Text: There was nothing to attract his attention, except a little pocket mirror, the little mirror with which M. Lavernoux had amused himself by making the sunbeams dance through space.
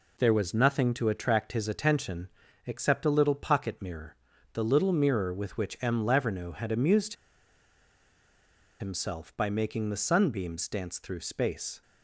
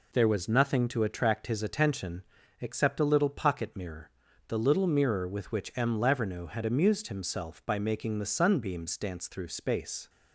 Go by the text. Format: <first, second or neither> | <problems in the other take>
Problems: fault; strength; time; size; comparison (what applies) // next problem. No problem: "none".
second | pauses between "amused" and "himself"; strong; at 7.1 s; 1.6 s long